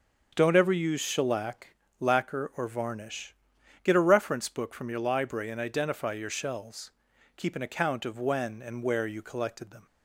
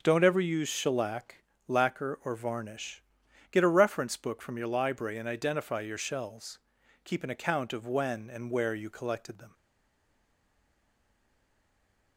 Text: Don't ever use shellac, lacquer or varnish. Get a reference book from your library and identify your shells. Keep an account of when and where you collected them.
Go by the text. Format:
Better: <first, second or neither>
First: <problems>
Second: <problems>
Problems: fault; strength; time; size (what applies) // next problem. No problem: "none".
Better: first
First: starts louder than the rest; until 1.3 s; 6 dB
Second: starts louder than the rest; until 1.0 s; 6.5 dB // stays silent after the last word; strong; from 9.5 s on; 2.6 s long